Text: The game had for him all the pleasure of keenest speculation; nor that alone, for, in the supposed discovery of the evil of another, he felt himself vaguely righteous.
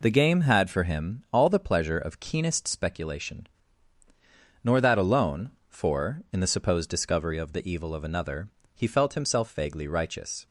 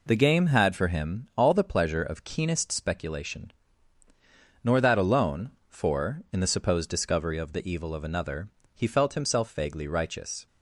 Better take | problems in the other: neither | none

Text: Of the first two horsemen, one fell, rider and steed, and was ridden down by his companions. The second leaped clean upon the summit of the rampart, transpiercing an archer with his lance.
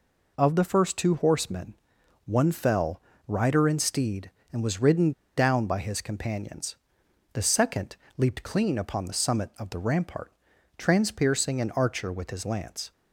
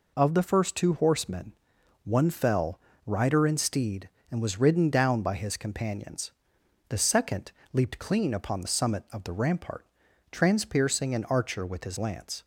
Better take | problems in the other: second | pauses between "ridden" and "down"; slight; at 5.1 s; 0.25 s long // pauses between "second" and "leaped"; slight; at 7.9 s; 0.22 s long; slight in the second

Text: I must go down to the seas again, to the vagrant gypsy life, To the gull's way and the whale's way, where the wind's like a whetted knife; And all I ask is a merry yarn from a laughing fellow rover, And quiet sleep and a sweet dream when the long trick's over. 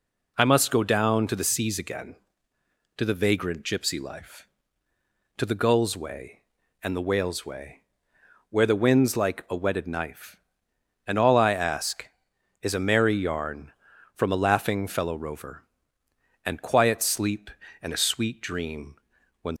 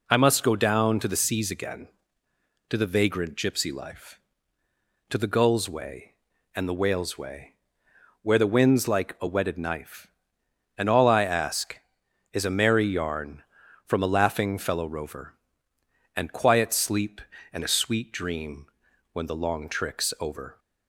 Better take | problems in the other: second | pauses between "dream" and "when"; noticeable; at 18.9 s; 0.46 s long; noticeable in the second // stops before "the long trick's over"; at 19.5 s

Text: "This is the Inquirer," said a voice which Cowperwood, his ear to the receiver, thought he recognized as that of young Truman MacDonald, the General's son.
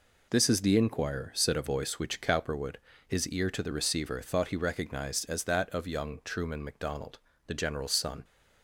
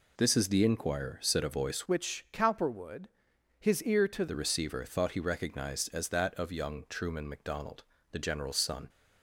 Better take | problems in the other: first | changes voice from "which" to "to"; from 1.8 to 4.2 s; 2.4 s long

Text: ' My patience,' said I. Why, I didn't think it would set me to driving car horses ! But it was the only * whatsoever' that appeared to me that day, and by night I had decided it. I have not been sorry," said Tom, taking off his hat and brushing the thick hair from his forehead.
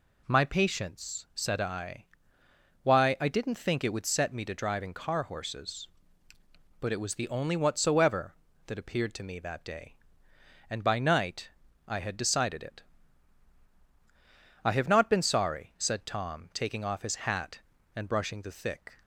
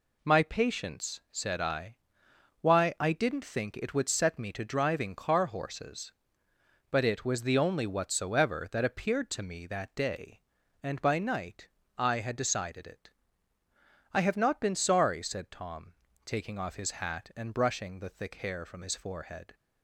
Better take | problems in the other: second | pauses between "night" and "I"; at 11.4 s; 0.38 s long; slight in the second // stops before "hair from his forehead"; at 19.0 s

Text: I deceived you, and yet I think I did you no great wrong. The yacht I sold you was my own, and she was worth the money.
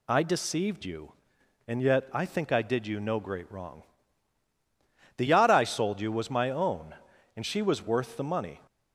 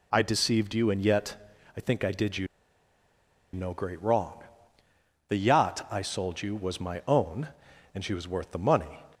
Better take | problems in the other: first | pauses between "yet" and "I"; at 1.3 s; 0.40 s long // pauses between "you" and "no"; at 2.4 s; 1.0 s long

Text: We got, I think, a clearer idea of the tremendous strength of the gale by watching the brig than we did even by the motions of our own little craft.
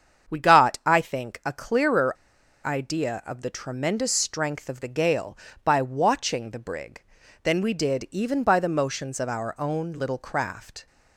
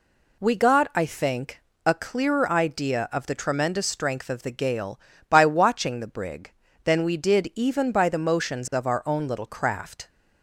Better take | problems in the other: second | starts louder than the rest; strong; until 1.3 s; 7.5 dB // pauses between "clearer" and "idea"; noticeable; at 2.1 s; 0.53 s long

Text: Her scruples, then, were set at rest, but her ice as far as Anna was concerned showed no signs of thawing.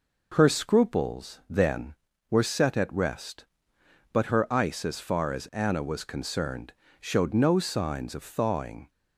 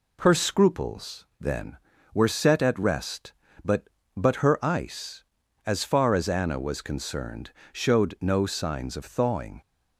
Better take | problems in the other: first | says "but" twice; at 4.1 s // pauses between "concerned" and "showed"; slight; at 7.5 s; 0.20 s long; slight in the first

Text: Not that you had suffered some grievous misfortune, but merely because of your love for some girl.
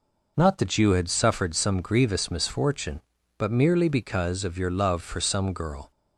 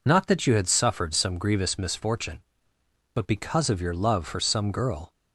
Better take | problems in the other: first | skips "merely"; at 3.2 s

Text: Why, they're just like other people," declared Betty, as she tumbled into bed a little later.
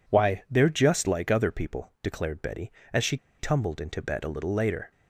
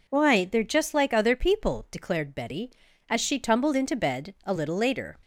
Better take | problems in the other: second | pauses between "she" and "tumbled"; slight; at 3.1 s; 0.23 s long

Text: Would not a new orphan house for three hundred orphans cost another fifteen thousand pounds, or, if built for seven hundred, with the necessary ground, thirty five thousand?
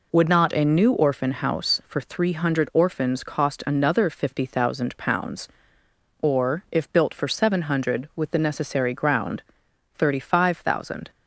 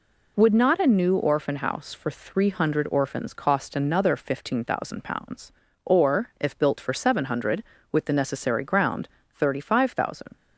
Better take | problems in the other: second | says "fifty" for "fifteen"; at 4.0 s

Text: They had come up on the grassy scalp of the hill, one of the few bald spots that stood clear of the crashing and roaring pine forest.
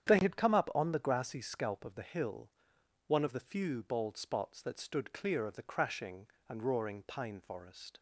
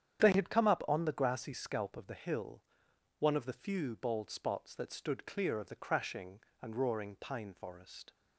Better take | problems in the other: neither | starts louder than the rest; strong; the same in both

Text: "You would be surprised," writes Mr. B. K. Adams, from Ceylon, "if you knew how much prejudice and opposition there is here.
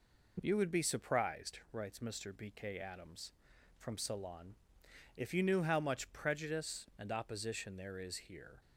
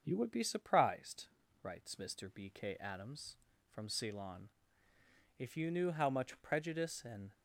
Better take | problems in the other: first | starts louder than the rest; until 1.0 s; 6.5 dB // stops before "opposition there is here"; at 7.3 s

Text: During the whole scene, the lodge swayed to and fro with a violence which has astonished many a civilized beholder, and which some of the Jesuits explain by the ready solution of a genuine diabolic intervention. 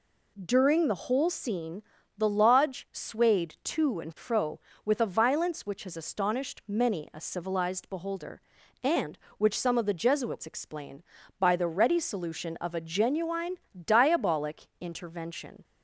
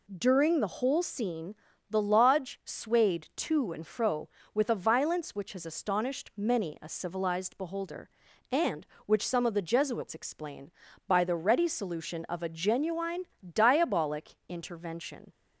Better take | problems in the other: neither | pauses between "genuine" and "diabolic"; slight; the same in both

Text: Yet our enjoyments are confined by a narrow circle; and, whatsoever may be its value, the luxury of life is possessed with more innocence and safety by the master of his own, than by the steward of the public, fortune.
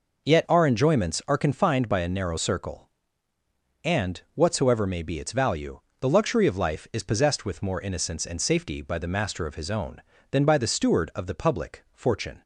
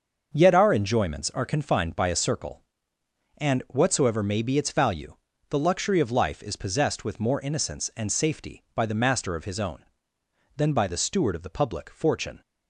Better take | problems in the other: first | starts louder than the rest; until 1.3 s; 6.5 dB // skips "narrow"; at 2.1 s

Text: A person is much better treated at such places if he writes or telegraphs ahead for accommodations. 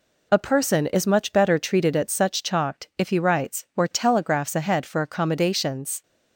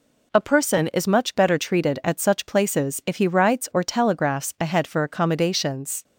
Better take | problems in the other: second | says "chalked" for "places"; at 2.4 s

